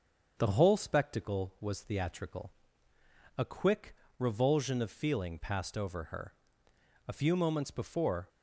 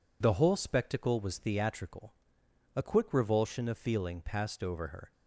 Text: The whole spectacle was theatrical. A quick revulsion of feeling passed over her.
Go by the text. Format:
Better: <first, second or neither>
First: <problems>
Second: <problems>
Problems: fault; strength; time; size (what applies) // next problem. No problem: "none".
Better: second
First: starts louder than the rest; until 1.3 s; 6.5 dB // pauses between "quick" and "revulsion"; slight; at 3.9 s; 0.24 s long // goes on to say "A few moments before"; noticeable; from 7.0 s on; 1.2 s long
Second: none